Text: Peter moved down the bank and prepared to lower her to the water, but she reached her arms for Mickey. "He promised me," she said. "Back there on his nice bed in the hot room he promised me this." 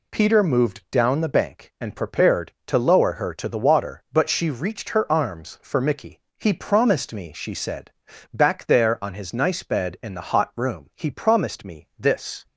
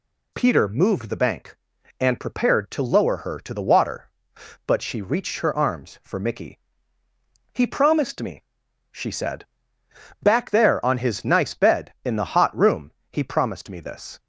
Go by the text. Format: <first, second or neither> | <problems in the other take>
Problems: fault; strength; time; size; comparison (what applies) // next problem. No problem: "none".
first | skips "down"; at 1.0 s // pauses between "room" and "he"; slight; at 12.9 s; 0.20 s long